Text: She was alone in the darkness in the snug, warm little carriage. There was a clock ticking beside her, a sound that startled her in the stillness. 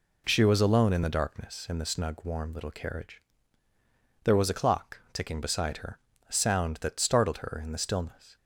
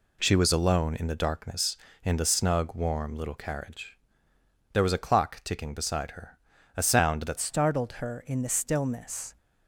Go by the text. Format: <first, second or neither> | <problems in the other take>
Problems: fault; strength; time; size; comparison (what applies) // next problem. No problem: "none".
first | changes voice at "startled"; from 7.3 s on; 2.0 s long